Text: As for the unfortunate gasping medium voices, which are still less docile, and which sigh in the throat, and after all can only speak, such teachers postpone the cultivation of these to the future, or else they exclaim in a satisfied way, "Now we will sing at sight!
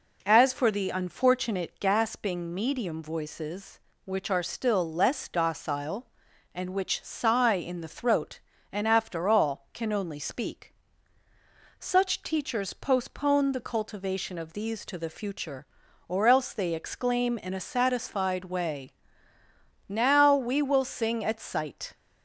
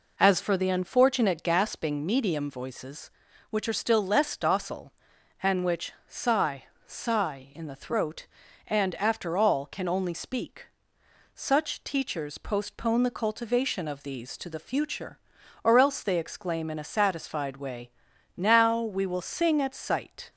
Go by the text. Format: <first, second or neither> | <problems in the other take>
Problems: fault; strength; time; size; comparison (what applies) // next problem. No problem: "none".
first | says "sigh" twice; at 6.8 s